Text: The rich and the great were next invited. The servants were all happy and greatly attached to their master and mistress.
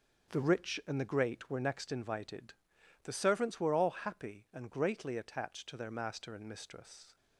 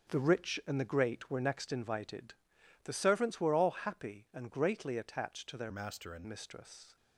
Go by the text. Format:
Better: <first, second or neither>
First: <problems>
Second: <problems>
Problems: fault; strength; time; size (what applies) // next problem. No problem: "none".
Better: first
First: starts louder than the rest; until 1.4 s; 7 dB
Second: starts louder than the rest; strong; until 1.1 s; 7 dB // changes voice from "master" to "and"; from 5.7 to 6.2 s; 0.5 s long